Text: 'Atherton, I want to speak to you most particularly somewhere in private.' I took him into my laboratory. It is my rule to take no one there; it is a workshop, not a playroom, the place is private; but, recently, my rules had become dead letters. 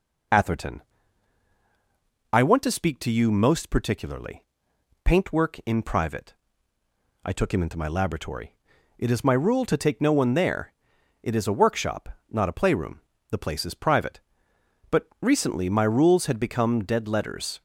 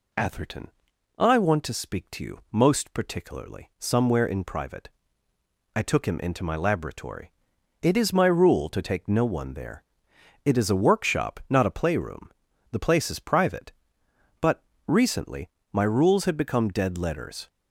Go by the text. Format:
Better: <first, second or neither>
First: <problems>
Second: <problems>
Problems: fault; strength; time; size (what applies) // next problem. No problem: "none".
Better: second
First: says "paintwork" for "somewhere"; at 5.0 s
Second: none